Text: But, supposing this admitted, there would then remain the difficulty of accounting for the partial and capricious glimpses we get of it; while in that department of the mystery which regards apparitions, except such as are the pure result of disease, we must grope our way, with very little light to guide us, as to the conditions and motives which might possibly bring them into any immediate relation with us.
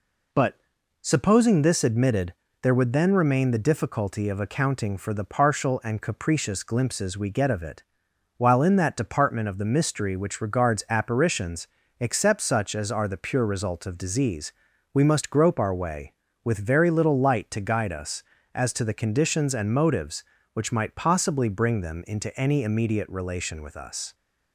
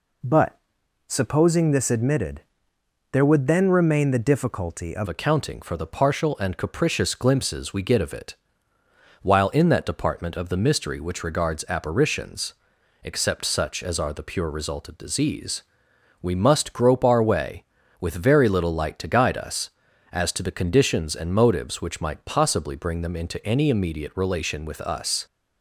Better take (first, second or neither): first